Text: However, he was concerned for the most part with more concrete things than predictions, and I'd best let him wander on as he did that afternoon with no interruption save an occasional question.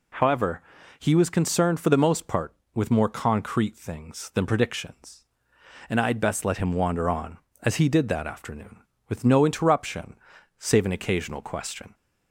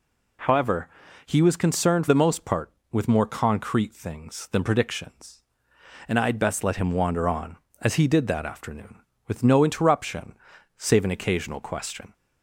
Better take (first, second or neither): first